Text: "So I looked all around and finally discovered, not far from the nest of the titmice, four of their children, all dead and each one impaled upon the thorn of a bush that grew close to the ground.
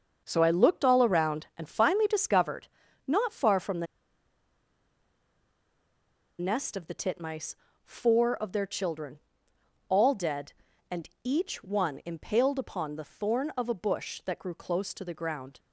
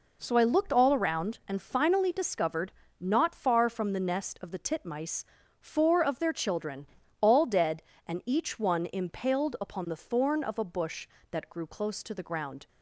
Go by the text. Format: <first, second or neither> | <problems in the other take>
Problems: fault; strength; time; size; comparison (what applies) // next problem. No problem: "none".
second | starts louder than the rest; until 1.2 s; 6.5 dB // pauses between "the" and "nest"; strong; at 3.8 s; 2.5 s long // pauses between "and" and "each"; slight; at 11.0 s; 0.16 s long